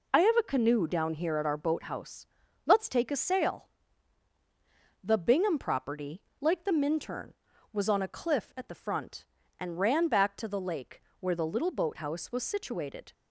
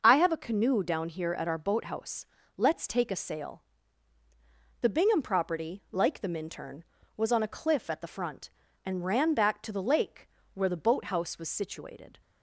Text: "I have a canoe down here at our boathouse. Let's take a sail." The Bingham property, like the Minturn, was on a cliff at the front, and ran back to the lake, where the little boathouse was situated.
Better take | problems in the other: first | starts louder than the rest; noticeable; until 1.0 s; 6 dB // skips "little"; at 10.7 s

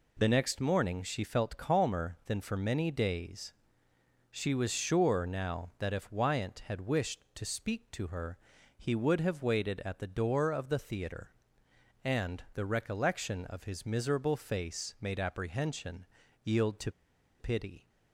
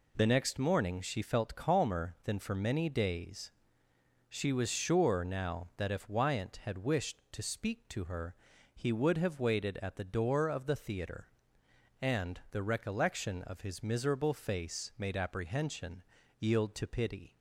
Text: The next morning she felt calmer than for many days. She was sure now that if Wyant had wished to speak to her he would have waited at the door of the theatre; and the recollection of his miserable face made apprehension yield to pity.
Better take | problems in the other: second | pauses between "her" and "he"; at 8.3 s; 0.40 s long; also in the second // pauses between "apprehension" and "yield"; at 16.0 s; 0.40 s long; also in the second // pauses between "to" and "pity"; noticeable; at 16.8 s; 0.49 s long

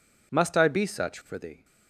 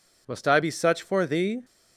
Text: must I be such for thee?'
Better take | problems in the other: neither | none

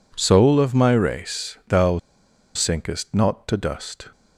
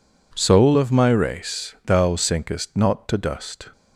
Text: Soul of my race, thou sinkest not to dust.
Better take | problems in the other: second | pauses between "thou" and "sinkest"; noticeable; at 1.9 s; 0.58 s long

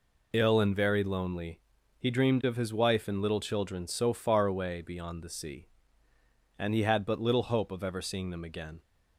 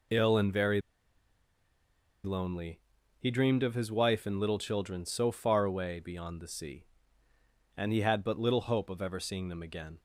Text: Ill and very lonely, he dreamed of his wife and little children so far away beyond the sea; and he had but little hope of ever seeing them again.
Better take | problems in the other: first | pauses between "very" and "lonely"; strong; at 0.8 s; 1.4 s long

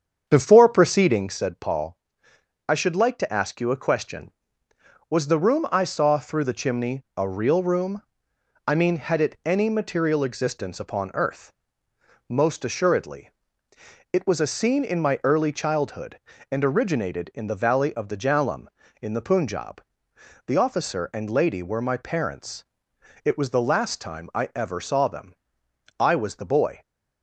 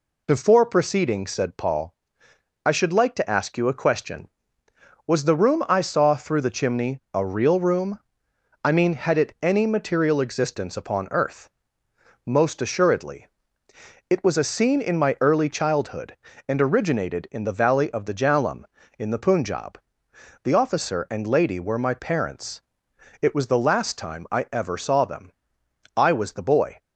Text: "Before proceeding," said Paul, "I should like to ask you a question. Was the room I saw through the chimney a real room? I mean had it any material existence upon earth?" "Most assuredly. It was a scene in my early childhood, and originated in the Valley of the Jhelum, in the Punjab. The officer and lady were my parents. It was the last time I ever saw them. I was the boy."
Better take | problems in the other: second | starts louder than the rest; strong; until 1.3 s; 7.5 dB

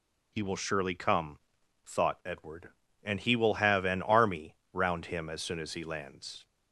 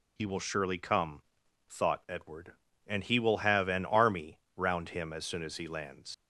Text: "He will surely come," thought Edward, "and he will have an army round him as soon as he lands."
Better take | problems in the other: first | pauses between "army" and "round"; slight; at 4.4 s; 0.16 s long; slight in the first // leaves "lands" unfinished; at 6.1 s; 155 ms

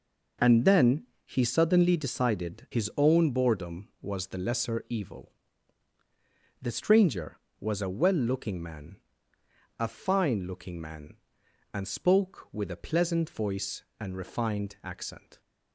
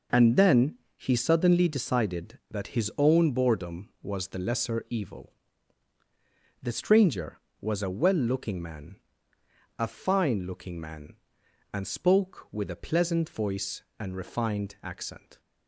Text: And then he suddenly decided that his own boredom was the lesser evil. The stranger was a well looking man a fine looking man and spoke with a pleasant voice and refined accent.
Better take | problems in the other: second | pauses between "then" and "he"; slight; at 1.0 s; 0.20 s long; slight in the second // skips "that"; at 2.7 s // pauses between "man" and "a"; noticeable; at 8.9 s; 0.82 s long; noticeable in the second

